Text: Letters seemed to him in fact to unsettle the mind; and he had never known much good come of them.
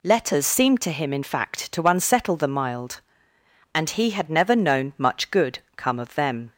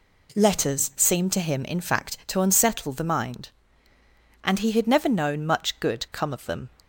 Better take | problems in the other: second | says "mild" for "mind"; at 2.4 s // pauses between "good" and "come"; slight; at 5.5 s; 0.18 s long

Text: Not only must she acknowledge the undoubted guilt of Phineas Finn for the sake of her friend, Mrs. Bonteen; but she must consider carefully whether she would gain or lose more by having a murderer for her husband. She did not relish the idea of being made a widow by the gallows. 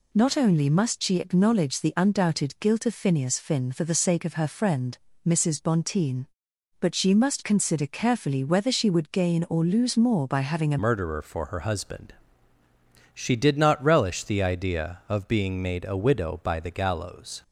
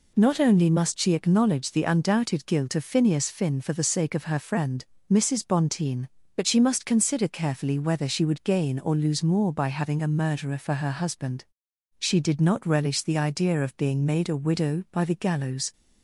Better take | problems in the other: second | changes voice at "murderer"; from 10.8 s on; 6.6 s long

